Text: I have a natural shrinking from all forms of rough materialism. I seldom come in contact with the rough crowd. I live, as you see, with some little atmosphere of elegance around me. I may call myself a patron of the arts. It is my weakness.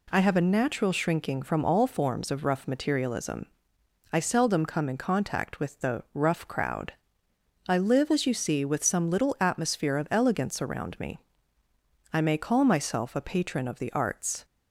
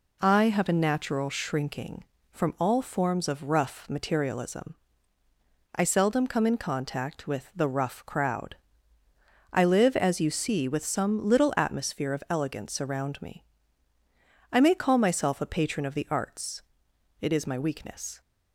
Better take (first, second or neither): second